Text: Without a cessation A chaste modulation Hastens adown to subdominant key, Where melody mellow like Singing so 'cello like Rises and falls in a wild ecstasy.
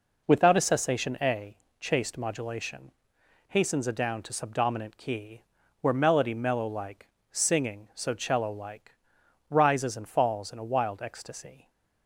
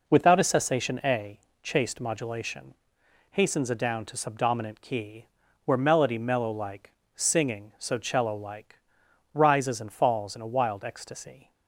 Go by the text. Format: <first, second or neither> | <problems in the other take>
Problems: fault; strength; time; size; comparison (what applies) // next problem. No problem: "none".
neither | pauses between "A" and "chaste"; slight; the same in both // pauses between "modulation" and "Hastens"; noticeable; the same in both // pauses between "like" and "Singing"; slight; the same in both // pauses between "like" and "Rises"; noticeable; the same in both